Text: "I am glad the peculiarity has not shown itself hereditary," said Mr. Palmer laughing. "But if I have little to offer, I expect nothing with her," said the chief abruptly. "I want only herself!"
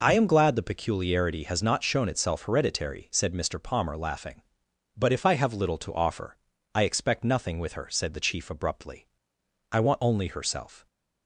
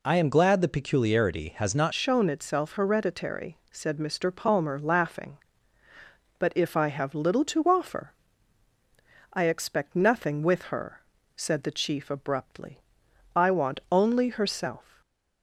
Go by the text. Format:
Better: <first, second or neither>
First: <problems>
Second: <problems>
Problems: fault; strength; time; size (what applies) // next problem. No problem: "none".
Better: first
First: none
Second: changes voice at "shown"; from 1.9 s on; 13.1 s long // stays silent after the last word; slight; from 14.8 s on; 0.6 s long